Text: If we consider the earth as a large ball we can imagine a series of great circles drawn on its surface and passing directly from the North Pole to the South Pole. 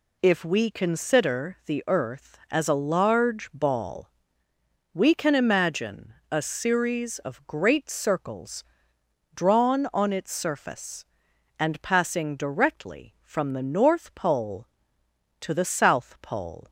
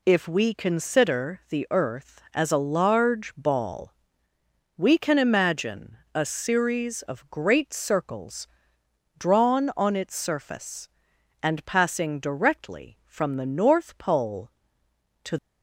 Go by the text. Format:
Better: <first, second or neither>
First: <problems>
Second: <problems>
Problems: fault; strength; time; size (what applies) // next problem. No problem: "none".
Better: first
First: pauses between "ball" and "we"; noticeable; at 4.0 s; 0.84 s long // pauses between "imagine" and "a"; slight; at 6.1 s; 0.18 s long // pauses between "circles" and "drawn"; noticeable; at 8.6 s; 0.68 s long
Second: pauses between "ball" and "we"; noticeable; at 3.9 s; 0.84 s long // pauses between "imagine" and "a"; slight; at 5.9 s; 0.18 s long // pauses between "circles" and "drawn"; noticeable; at 8.4 s; 0.68 s long // stops before "the South Pole"; at 15.3 s